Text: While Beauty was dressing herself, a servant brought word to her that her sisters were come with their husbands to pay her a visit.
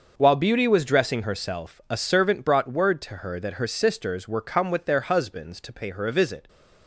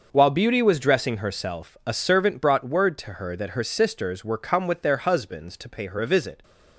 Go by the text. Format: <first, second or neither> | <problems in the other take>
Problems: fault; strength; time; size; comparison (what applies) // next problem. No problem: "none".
neither | starts louder than the rest; the same in both